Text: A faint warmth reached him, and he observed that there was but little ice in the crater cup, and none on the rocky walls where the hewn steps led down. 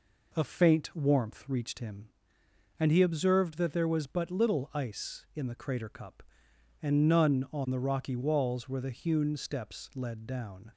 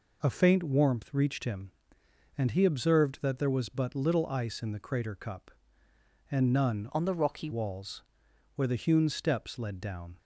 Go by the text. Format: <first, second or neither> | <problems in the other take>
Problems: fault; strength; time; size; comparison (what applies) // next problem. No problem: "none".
first | changes voice from "on" to "rocky"; from 6.9 to 7.5 s; 0.6 s long // pauses between "walls" and "where"; noticeable; at 8.0 s; 0.54 s long